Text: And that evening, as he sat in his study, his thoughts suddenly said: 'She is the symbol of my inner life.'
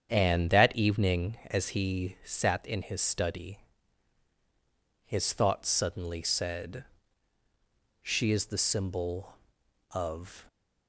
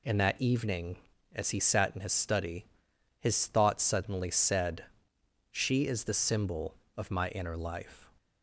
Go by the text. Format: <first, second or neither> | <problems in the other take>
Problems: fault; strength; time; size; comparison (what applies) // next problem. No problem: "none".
second | starts louder than the rest; strong; until 1.1 s; 8 dB // stops before "my inner life"; at 10.4 s